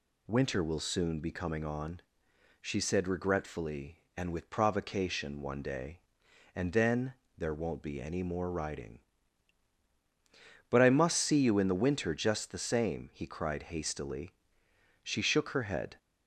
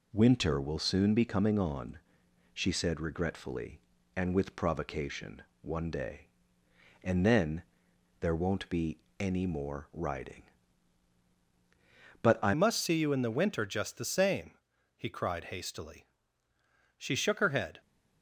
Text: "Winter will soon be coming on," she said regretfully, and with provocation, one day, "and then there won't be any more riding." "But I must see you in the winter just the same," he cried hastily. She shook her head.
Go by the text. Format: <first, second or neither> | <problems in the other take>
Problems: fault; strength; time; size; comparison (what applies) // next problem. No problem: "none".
first | pauses between "then" and "there"; noticeable; at 7.6 s; 0.58 s long; slight in the first // pauses between "be" and "any"; slight; at 9.0 s; 0.18 s long // changes voice at "must"; from 12.5 s on; 5.3 s long